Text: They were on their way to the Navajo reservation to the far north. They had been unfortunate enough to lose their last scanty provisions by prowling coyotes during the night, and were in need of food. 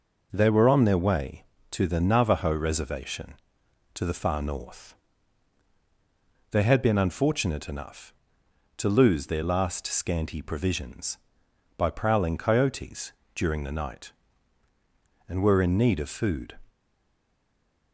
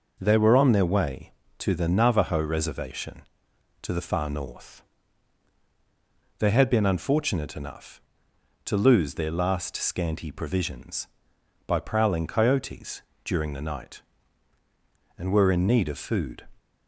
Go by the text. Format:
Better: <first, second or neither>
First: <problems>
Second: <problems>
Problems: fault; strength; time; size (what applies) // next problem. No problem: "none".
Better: second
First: pauses between "coyotes" and "during"; slight; at 13.1 s; 0.22 s long // stays silent after the last word; noticeable; from 16.6 s on; 1.3 s long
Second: pauses between "coyotes" and "during"; slight; at 13.0 s; 0.22 s long